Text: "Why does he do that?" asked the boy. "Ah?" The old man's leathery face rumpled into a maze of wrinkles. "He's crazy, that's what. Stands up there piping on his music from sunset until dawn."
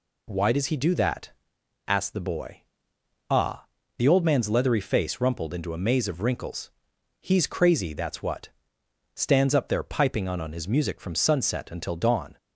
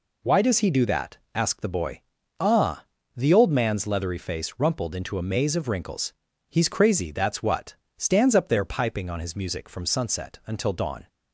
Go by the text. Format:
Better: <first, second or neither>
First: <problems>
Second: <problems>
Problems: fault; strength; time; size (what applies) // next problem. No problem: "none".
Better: second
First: says "on" twice; at 10.3 s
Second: none